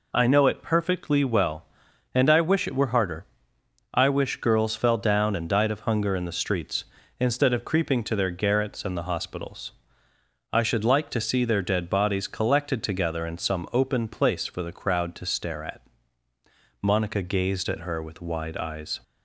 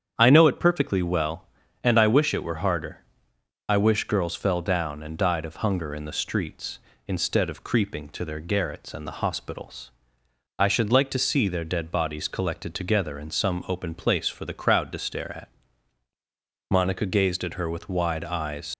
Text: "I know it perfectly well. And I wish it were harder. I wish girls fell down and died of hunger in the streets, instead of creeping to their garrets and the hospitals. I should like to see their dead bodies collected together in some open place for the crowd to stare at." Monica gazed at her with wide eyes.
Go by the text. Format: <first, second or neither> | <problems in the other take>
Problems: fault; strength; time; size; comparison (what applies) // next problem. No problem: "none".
first | starts louder than the rest; strong; until 1.1 s; 8 dB // leaves "eyes" unfinished; at 18.7 s; 80 ms